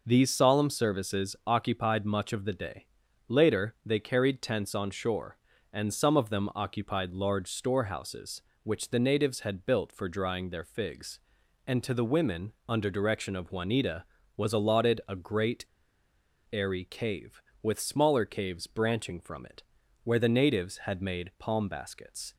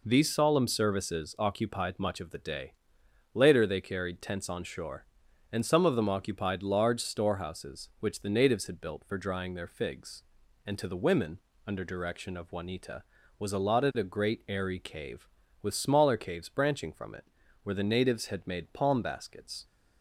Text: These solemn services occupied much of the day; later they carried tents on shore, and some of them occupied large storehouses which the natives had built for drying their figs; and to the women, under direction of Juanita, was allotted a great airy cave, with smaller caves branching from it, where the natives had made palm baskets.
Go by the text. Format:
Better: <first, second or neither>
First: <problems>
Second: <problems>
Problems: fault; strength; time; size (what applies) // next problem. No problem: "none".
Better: second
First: pauses between "great" and "airy"; noticeable; at 15.6 s; 0.86 s long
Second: none